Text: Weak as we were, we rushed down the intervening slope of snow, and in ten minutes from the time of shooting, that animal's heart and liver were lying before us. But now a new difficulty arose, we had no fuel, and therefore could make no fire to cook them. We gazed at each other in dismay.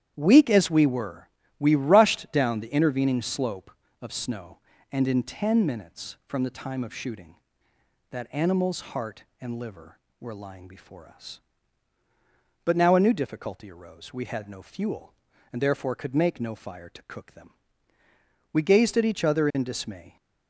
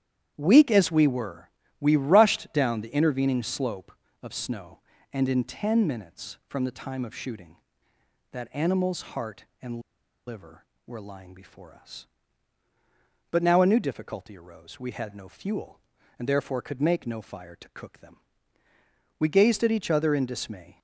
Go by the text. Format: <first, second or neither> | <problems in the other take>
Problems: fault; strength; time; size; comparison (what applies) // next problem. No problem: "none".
first | starts louder than the rest; strong; until 1.3 s; 10 dB; strong in the first // pauses between "and" and "liver"; noticeable; at 9.7 s; 0.48 s long